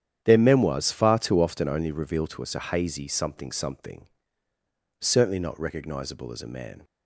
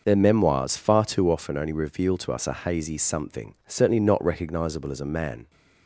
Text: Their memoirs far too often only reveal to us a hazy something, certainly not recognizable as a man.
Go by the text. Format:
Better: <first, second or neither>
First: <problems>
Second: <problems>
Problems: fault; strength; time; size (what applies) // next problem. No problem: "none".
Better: second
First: starts louder than the rest; strong; until 1.2 s; 9.5 dB // says "something" twice; at 3.4 s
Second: none